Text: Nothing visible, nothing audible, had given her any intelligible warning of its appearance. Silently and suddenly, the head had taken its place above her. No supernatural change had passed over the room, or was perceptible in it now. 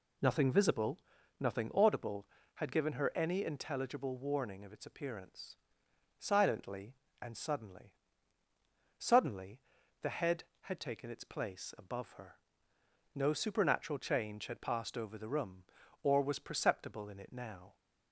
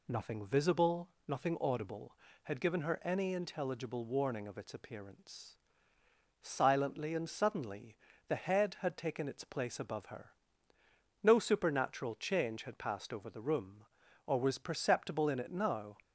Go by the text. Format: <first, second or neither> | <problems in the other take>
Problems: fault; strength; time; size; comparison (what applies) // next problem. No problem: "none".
second | says "suddenly" twice; at 9.0 s